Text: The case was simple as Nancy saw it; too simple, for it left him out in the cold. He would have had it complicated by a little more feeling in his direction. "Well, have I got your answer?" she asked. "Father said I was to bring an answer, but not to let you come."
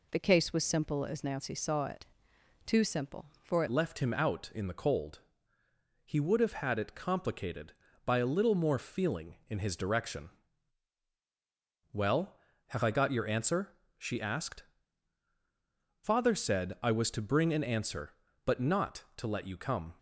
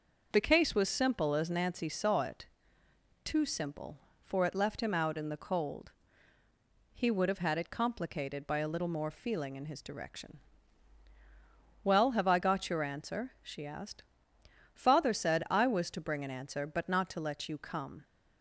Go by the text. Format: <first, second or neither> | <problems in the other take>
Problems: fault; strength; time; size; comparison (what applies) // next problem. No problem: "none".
second | changes voice at "left"; from 3.6 s on; 16.3 s long